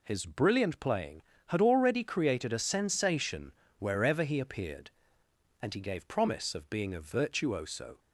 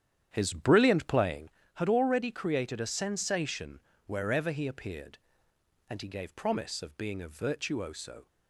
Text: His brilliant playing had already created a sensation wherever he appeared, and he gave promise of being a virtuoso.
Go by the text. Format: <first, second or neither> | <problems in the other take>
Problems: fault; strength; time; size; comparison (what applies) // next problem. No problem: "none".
first | starts louder than the rest; strong; until 1.6 s; 9.5 dB // pauses between "sensation" and "wherever"; slight; at 3.8 s; 0.26 s long; slight in the first